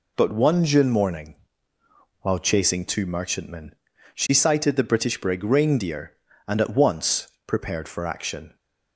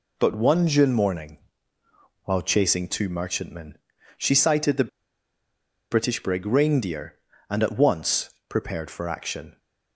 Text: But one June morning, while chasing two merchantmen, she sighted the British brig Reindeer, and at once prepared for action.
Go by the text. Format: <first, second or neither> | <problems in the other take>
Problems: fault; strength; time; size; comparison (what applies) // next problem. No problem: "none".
first | pauses between "the" and "British"; at 4.8 s; 1.0 s long // pauses between "once" and "prepared"; slight; at 8.2 s; 0.18 s long; slight in the first